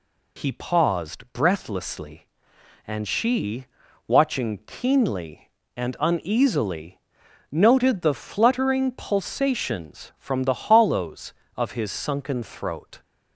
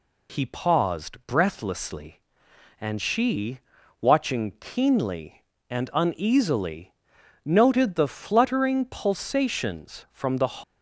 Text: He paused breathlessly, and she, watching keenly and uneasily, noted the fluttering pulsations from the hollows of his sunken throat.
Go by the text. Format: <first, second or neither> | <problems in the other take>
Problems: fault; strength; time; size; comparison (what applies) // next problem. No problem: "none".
first | stops before "hollows of his sunken throat"; at 10.6 s